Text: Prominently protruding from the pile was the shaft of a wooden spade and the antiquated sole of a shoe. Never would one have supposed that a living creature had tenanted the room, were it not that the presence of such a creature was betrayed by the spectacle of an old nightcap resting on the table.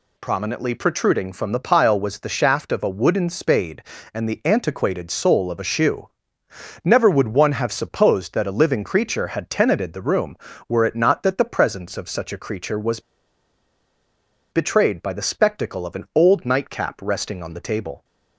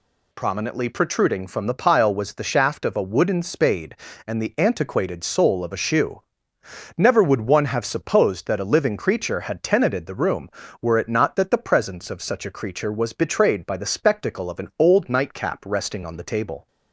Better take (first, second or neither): second